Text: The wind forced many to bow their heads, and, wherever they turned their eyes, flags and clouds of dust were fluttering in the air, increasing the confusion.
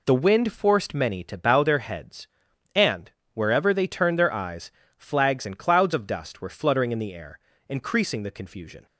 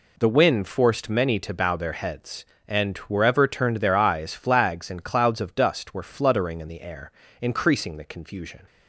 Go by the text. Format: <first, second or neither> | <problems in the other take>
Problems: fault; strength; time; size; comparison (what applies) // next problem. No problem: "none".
first | skips "they"; at 3.4 s